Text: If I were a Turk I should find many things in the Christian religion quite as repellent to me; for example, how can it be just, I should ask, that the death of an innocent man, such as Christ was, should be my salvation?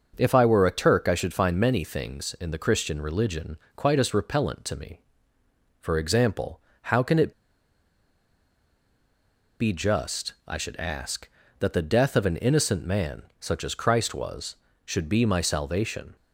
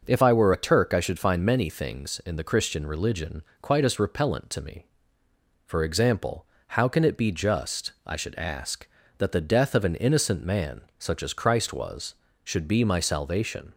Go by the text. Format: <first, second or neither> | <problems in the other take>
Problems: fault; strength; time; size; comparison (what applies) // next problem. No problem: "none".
second | starts louder than the rest; noticeable; until 1.1 s; 6 dB // pauses between "religion" and "quite"; slight; at 3.5 s; 0.18 s long; slight in the second // pauses between "it" and "be"; strong; at 7.3 s; 2.2 s long